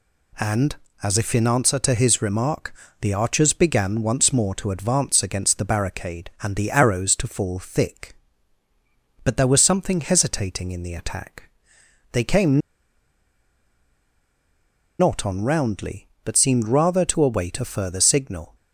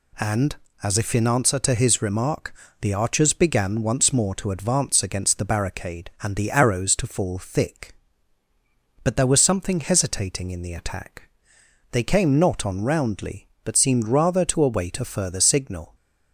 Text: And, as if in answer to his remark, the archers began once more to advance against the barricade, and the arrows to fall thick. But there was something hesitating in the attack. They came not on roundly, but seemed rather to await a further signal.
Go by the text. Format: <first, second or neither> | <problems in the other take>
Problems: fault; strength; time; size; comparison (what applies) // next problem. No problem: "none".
second | pauses between "came" and "not"; strong; at 12.5 s; 2.3 s long